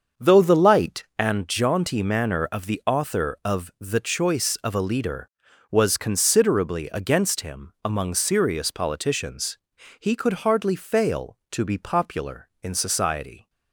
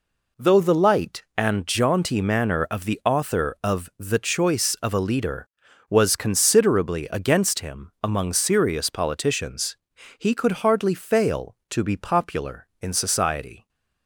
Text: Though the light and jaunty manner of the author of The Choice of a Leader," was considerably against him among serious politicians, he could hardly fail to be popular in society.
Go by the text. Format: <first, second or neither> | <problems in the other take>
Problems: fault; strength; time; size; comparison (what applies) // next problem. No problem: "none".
second | starts louder than the rest; until 1.3 s; 6.5 dB